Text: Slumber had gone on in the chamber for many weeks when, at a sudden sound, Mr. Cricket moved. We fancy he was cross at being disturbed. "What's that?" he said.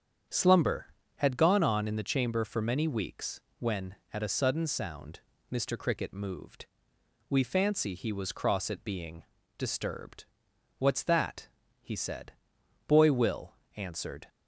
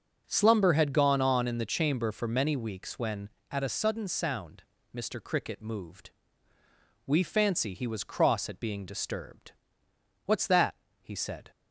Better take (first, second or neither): second